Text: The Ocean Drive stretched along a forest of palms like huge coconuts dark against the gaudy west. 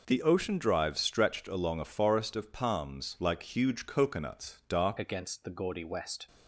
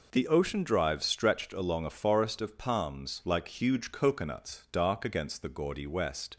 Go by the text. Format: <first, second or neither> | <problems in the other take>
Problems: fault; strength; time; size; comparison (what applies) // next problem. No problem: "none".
second | changes voice at "against"; from 4.9 s on; 1.3 s long